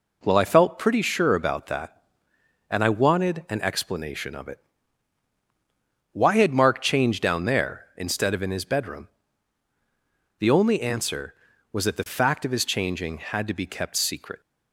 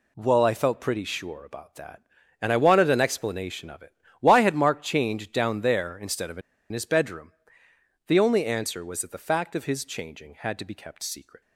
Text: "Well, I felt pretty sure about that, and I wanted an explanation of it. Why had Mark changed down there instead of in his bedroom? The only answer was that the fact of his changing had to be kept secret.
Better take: first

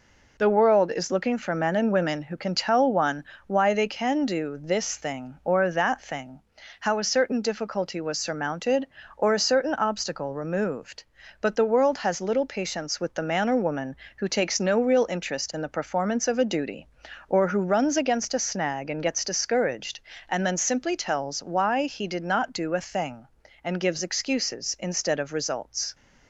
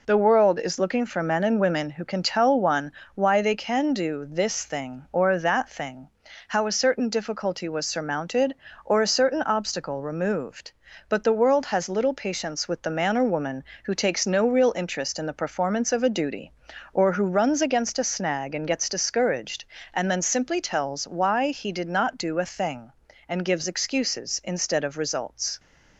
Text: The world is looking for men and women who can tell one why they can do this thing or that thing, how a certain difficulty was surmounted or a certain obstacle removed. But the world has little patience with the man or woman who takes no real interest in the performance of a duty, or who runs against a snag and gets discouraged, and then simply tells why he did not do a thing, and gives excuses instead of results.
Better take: neither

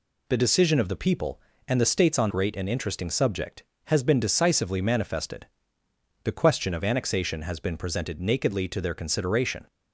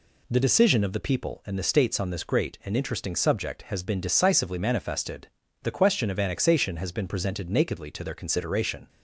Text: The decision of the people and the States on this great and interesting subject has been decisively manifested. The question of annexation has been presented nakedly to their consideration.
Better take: second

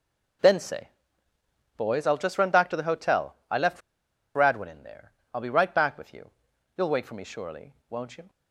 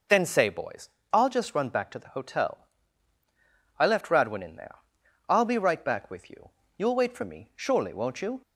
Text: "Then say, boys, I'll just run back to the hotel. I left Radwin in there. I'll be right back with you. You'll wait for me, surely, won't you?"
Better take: second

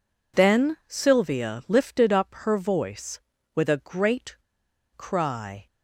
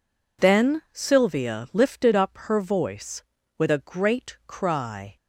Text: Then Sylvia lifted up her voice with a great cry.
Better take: second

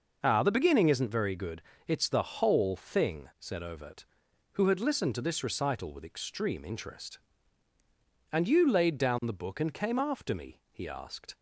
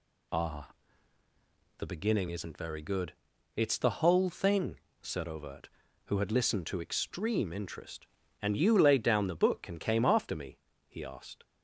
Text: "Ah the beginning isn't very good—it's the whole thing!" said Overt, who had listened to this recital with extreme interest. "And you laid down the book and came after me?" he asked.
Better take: first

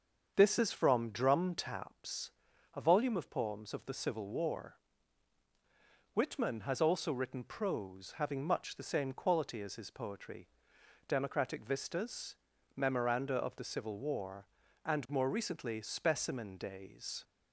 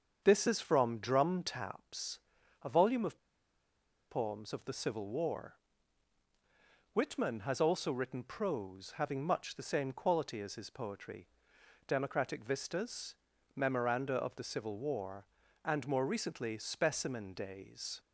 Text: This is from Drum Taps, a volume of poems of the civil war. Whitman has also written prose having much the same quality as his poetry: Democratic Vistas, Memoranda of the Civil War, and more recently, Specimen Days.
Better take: first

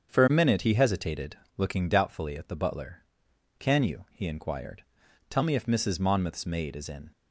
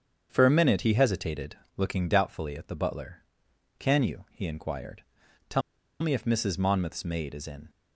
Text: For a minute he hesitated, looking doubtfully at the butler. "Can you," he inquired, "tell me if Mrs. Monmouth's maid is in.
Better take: first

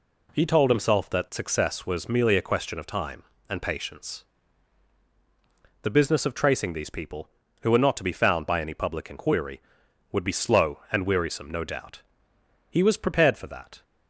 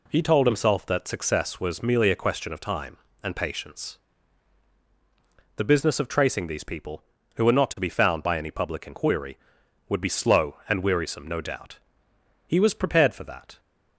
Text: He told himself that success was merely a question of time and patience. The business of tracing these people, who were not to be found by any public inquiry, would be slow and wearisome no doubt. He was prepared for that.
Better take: neither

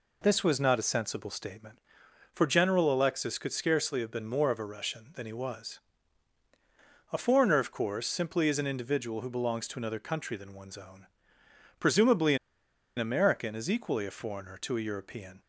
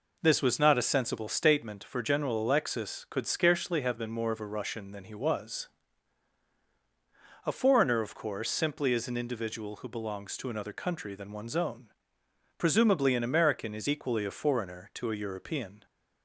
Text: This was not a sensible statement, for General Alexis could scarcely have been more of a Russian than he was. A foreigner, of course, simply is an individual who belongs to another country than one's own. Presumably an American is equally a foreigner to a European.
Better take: second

